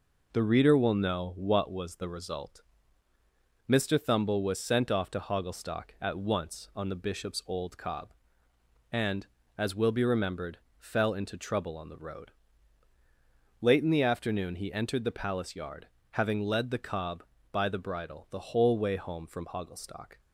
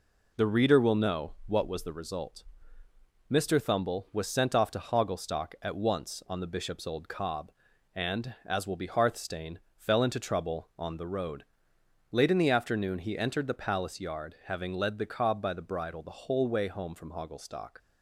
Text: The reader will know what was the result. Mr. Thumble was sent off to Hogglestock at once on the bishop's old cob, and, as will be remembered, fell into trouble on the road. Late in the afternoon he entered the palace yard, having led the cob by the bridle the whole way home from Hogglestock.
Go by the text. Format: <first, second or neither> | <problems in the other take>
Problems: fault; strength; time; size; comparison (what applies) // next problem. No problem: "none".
first | says "hearthstane" for "remembered"; at 8.8 s